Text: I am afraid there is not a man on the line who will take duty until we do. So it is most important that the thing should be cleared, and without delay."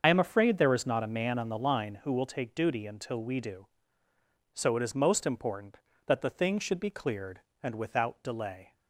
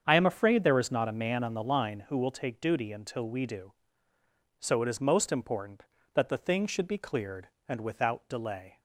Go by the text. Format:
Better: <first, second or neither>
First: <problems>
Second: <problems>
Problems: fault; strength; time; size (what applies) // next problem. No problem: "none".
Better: second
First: loses the start of "I"; at 0.0 s; 60 ms // starts louder than the rest; until 1.0 s; 6.5 dB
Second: starts louder than the rest; strong; until 1.0 s; 7 dB